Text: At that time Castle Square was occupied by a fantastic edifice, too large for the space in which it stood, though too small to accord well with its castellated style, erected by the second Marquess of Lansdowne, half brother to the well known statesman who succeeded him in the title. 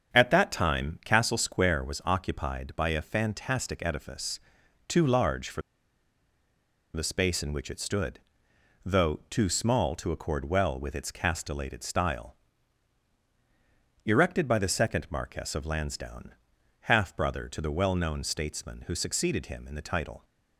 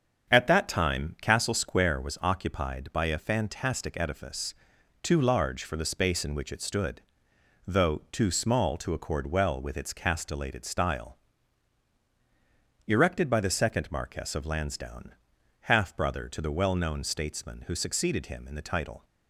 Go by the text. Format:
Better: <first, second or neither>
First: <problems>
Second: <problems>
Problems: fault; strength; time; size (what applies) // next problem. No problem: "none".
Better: second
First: starts louder than the rest; strong; until 1.1 s; 7.5 dB // pauses between "for" and "the"; strong; at 5.6 s; 1.3 s long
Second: starts louder than the rest; strong; until 1.3 s; 7.5 dB